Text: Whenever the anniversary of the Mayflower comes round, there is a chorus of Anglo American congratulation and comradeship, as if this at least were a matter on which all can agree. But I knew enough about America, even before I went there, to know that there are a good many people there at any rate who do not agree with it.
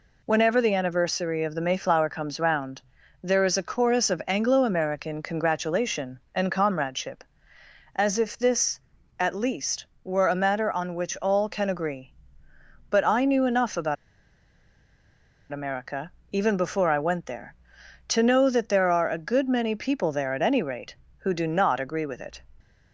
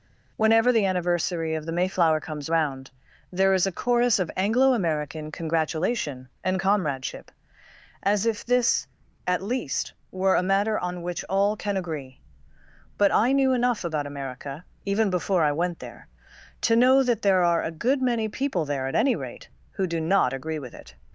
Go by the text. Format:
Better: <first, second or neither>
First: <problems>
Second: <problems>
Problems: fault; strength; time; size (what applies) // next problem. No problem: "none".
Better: second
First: pauses between "about" and "America"; strong; at 13.9 s; 1.5 s long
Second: none